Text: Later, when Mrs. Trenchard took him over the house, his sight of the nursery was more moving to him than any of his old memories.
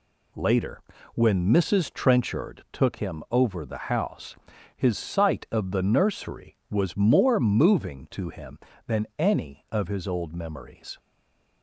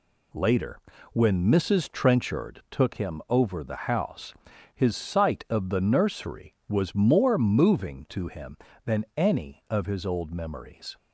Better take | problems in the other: second | stays silent after the last word; slight; from 10.9 s on; 0.7 s long

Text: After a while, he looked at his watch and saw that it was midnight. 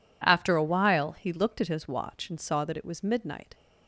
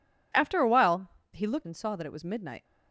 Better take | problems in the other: first | skips "at his watch"; at 1.6 s

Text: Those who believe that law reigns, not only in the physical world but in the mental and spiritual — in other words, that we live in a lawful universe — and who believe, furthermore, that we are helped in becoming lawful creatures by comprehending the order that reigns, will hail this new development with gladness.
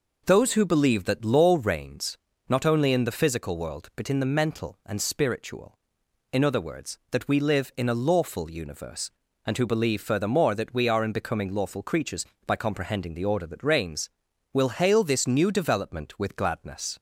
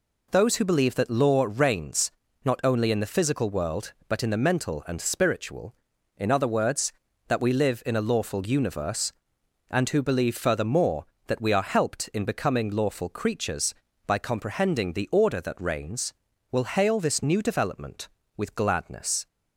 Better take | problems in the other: second | skips "helped"; at 11.0 s

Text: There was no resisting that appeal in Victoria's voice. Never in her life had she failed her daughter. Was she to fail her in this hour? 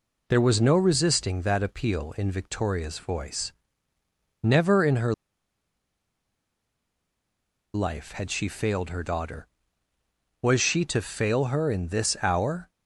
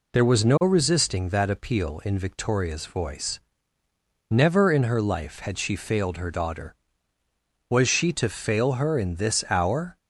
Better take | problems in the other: second | pauses between "her" and "life"; strong; at 5.1 s; 2.6 s long

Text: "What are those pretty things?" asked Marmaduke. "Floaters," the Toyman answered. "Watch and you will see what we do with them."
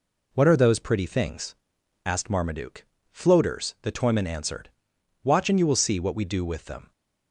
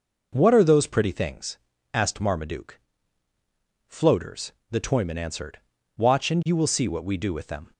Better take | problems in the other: neither | none

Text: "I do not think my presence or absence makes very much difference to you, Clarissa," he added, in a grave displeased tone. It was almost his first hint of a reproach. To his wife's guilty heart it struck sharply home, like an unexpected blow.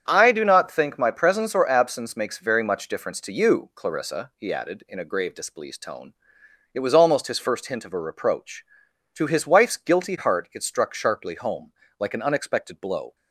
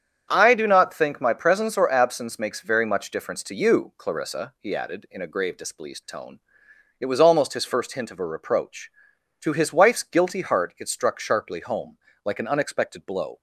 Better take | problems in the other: neither | starts louder than the rest; strong; the same in both

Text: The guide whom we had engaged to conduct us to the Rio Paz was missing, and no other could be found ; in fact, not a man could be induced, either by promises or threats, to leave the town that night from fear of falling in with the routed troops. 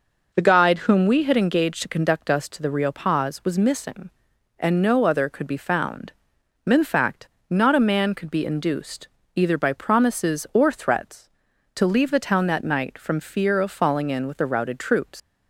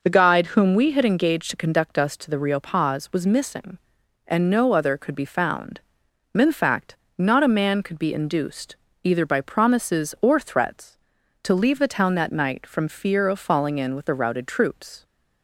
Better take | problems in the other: second | leaves "troops" unfinished; at 15.1 s; 160 ms

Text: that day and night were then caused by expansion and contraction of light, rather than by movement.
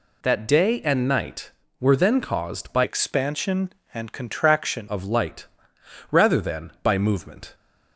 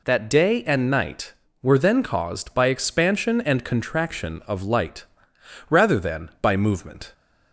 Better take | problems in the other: second | changes voice from "expansion" to "contraction"; from 2.8 to 4.8 s; 2.0 s long

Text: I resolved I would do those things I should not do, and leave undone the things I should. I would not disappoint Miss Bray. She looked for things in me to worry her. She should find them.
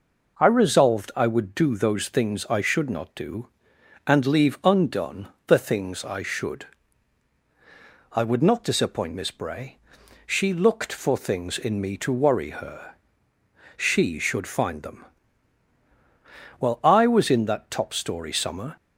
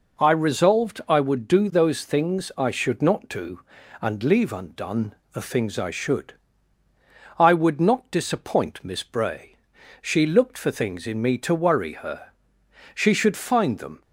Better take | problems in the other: second | pauses between "undone" and "the"; slight; at 5.2 s; 0.18 s long; slight in the second // goes on to say "Well I was in that top story summer"; strong; from 16.5 s on; 2.1 s long

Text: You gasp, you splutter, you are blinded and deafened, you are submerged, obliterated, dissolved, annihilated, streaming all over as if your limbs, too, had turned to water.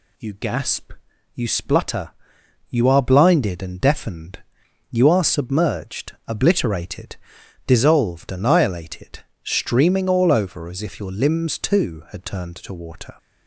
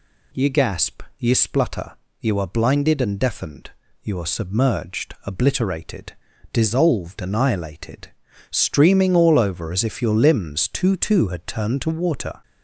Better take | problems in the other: first | says "too" twice; at 10.9 s

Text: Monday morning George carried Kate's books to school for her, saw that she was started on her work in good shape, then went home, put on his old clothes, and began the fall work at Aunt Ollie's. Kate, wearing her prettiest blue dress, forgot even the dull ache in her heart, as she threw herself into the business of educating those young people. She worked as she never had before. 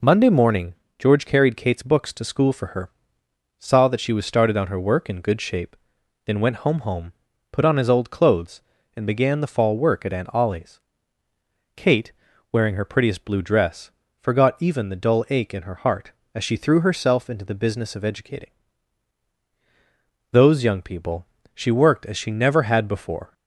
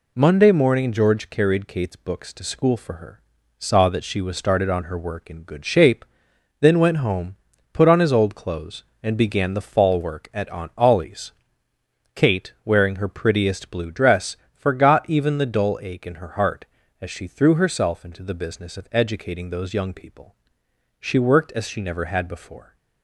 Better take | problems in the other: second | pauses between "morning" and "George"; slight; at 0.7 s; 0.24 s long // says "home" twice; at 6.8 s // pauses between "educating" and "those"; strong; at 18.5 s; 1.8 s long

